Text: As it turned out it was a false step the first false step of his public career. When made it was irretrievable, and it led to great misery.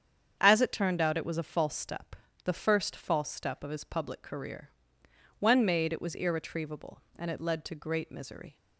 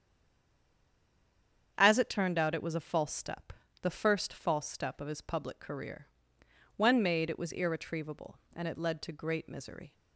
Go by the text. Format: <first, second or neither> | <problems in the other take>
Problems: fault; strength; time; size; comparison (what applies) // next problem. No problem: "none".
first | stays silent before the first word; noticeable; until 1.7 s; 1.7 s long // starts louder than the rest; strong; until 2.7 s; 8 dB; strong in the first // pauses between "step" and "the"; slight; at 3.5 s; 0.30 s long; slight in the first